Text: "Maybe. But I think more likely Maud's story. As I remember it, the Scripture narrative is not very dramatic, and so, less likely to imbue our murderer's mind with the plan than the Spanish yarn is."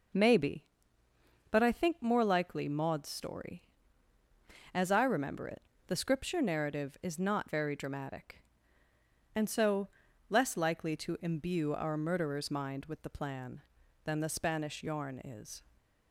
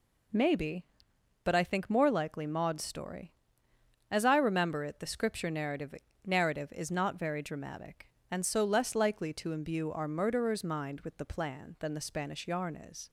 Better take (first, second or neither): first